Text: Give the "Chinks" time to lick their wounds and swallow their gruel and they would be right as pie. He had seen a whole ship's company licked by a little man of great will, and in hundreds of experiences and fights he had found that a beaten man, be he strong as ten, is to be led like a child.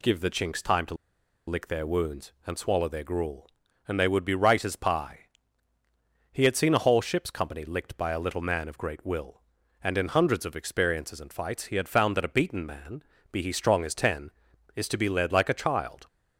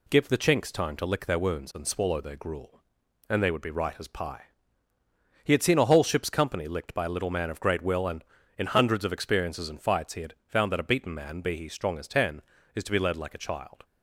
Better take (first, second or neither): second